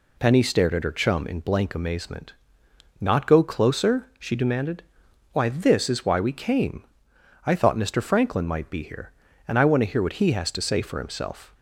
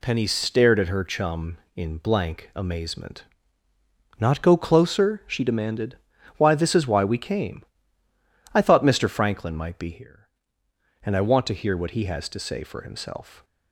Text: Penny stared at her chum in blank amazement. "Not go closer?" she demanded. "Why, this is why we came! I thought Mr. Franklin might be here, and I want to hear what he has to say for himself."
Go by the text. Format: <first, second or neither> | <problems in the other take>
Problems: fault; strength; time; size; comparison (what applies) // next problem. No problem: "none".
neither | none